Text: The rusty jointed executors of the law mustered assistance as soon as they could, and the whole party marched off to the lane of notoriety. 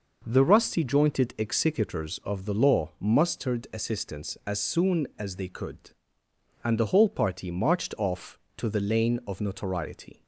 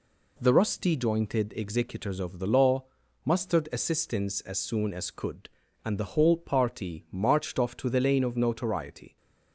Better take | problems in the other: first | pauses between "law" and "mustered"; at 2.8 s; 0.40 s long // skips "they"; at 5.1 s

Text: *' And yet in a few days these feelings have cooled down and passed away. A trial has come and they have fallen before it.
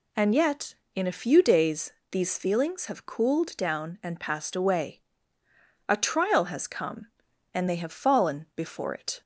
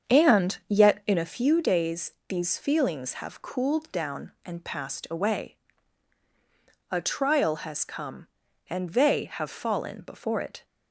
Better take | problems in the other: first | starts louder than the rest; strong; until 1.4 s; 7.5 dB // pauses between "days" and "these"; slight; at 2.1 s; 0.16 s long; slight in the first

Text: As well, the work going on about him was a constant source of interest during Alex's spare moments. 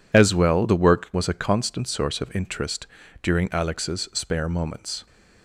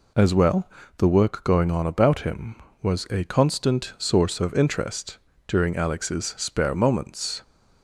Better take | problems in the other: second | skips "going on about him"; at 1.1 s // pauses between "interest" and "during"; slight; at 2.8 s; 0.36 s long; slight in the second

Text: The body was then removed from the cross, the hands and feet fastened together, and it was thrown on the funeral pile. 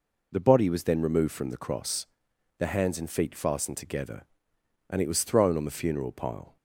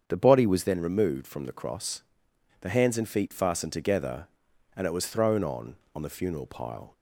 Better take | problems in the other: first | starts louder than the rest; strong; until 1.0 s; 7.5 dB // says "on" twice; at 5.9 s

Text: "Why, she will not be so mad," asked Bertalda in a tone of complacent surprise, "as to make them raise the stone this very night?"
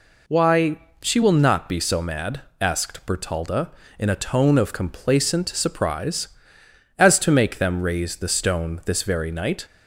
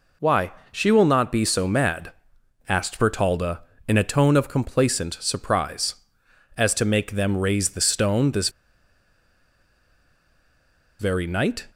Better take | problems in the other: first | pauses between "this" and "very"; strong; at 8.4 s; 2.5 s long

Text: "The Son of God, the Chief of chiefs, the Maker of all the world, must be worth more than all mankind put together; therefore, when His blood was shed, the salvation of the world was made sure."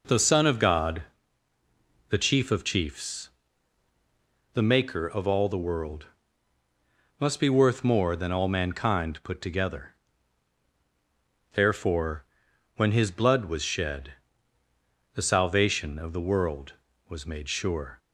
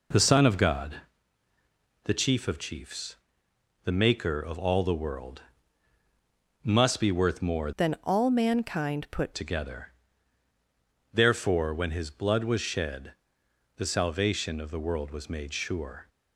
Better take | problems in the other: first | changes voice from "than" to "put"; from 7.7 to 9.3 s; 1.6 s long

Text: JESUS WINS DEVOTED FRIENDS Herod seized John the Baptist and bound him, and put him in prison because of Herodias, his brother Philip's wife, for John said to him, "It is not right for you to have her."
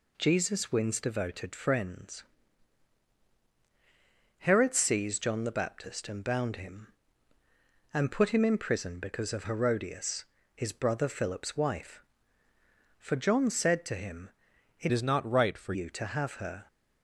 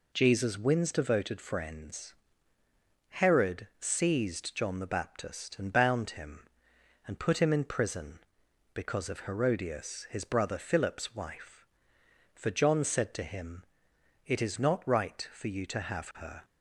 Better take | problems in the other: second | pauses between "FRIENDS" and "Herod"; strong; at 2.2 s; 2.1 s long; noticeable in the second // changes voice from "is" to "for"; from 14.9 to 15.7 s; 0.8 s long

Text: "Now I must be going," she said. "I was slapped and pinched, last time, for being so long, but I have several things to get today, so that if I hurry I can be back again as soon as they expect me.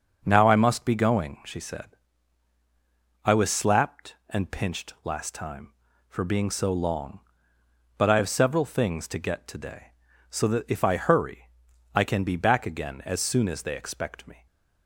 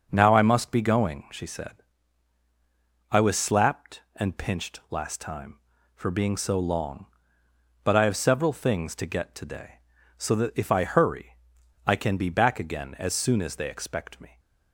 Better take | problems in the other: neither | starts louder than the rest; the same in both // pauses between "hurry" and "I"; noticeable; the same in both

